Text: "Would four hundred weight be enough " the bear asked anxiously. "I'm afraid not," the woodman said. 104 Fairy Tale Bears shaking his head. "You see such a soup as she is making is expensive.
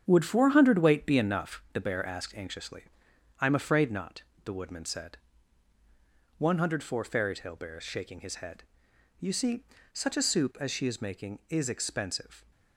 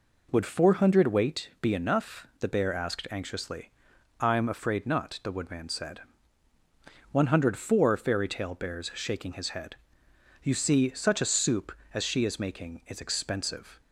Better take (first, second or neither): second